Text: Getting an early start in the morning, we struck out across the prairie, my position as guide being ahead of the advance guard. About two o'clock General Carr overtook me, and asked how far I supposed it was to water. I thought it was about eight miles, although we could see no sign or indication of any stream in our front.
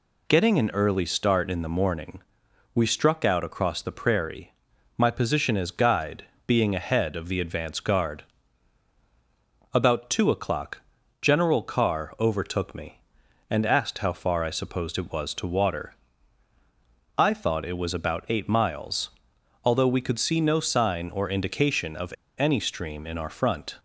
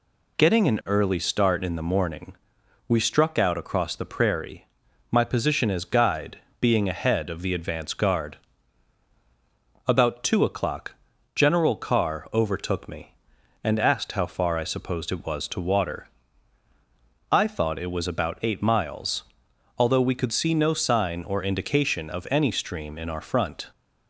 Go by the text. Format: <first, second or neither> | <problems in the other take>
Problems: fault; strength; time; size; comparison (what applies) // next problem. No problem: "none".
second | pauses between "guide" and "being"; slight; at 6.2 s; 0.24 s long; slight in the second // pauses between "o'clock" and "General"; at 10.8 s; 0.42 s long; also in the second // pauses between "of" and "any"; slight; at 22.1 s; 0.26 s long